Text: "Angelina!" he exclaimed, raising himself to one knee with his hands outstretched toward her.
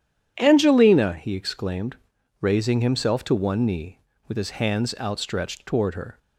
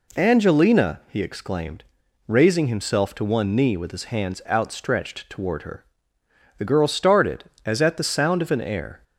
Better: first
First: none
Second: goes on to say "The girl started as at the sound of an air"; strong; from 6.5 s on; 2.4 s long

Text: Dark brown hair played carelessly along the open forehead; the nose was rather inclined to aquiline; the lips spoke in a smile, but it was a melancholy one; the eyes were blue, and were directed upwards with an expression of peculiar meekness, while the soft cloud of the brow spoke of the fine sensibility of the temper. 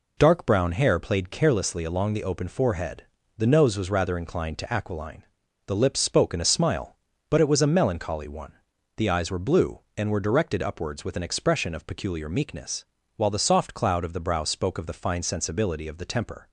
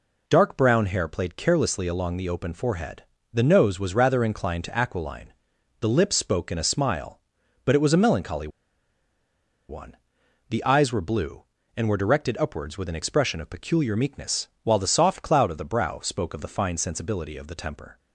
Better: first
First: none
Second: pauses between "melancholy" and "one"; at 8.4 s; 1.2 s long

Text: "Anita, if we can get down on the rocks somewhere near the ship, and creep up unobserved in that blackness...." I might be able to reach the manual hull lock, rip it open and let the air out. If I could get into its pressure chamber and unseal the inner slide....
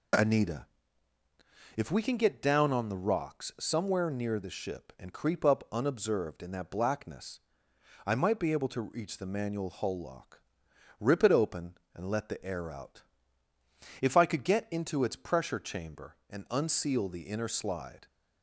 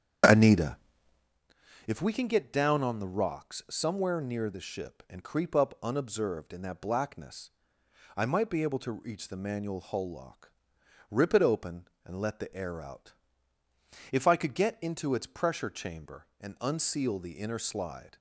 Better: first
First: none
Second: starts louder than the rest; until 1.4 s; 7 dB

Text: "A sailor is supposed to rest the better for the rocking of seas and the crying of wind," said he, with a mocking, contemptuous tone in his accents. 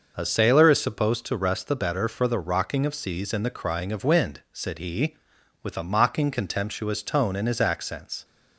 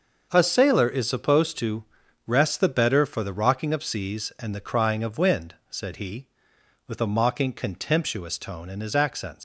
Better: first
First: none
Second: starts louder than the rest; noticeable; until 1.3 s; 6 dB // pauses between "to" and "rest"; at 1.8 s; 0.42 s long // leaves "accents" unfinished; at 9.3 s; 105 ms

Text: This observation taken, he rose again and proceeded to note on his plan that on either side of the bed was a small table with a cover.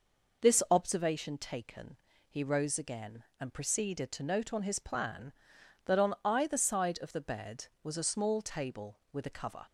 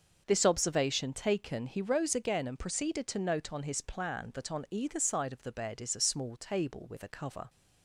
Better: first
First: none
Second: starts louder than the rest; until 1.2 s; 6 dB // says "is" for "was"; at 5.8 s

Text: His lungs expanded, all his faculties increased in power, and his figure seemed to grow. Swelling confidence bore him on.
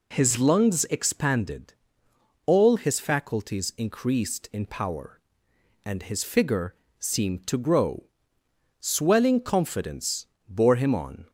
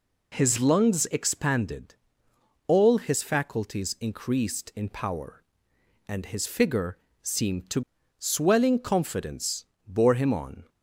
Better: first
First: pauses between "figure" and "seemed"; slight; at 6.7 s; 0.24 s long // pauses between "confidence" and "bore"; slight; at 10.2 s; 0.22 s long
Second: pauses between "figure" and "seemed"; slight; at 6.9 s; 0.24 s long // skips "grow"; at 7.9 s // pauses between "confidence" and "bore"; slight; at 9.6 s; 0.22 s long

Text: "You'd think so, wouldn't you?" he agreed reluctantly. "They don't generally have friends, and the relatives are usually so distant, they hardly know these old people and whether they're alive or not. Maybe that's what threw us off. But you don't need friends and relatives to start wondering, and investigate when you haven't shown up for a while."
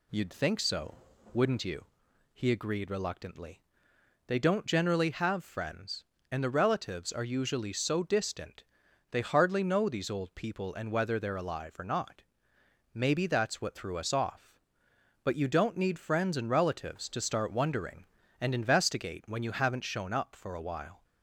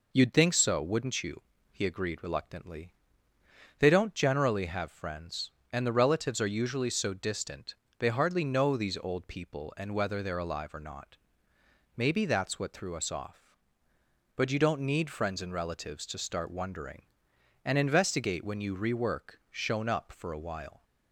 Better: first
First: none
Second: says "rework" for "haven't"; at 18.7 s

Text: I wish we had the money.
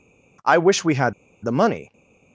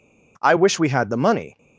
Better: second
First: pauses between "had" and "the"; slight; at 1.1 s; 0.31 s long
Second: none

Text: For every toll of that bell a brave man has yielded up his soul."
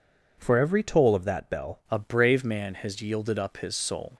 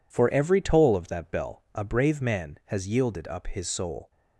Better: second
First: changes voice at "a"; from 1.9 s on; 2.2 s long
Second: none

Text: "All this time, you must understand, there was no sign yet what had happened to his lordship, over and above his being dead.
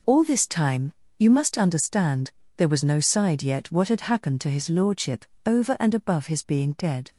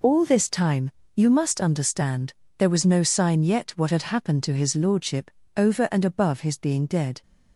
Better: second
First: says "side" for "sign"; at 2.9 s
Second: none

